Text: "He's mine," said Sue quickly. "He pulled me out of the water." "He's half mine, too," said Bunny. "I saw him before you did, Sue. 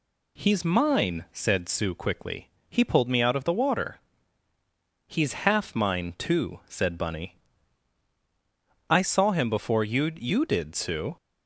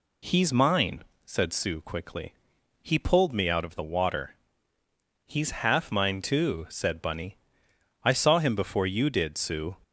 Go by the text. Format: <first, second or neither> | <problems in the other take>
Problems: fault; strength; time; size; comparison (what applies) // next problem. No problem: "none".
second | says "you" twice; at 10.1 s